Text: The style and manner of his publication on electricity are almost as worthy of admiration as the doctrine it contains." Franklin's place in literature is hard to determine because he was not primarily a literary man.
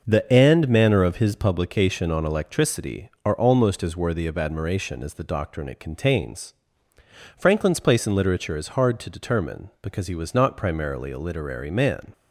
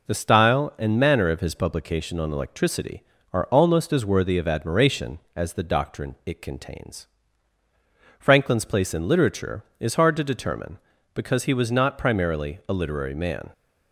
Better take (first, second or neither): second